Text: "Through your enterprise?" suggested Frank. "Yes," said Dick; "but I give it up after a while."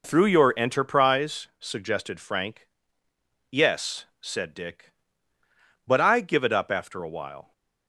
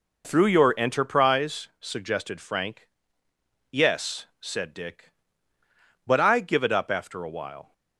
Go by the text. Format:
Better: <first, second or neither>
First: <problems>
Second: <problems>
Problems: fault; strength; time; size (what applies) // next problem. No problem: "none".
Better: neither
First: none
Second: none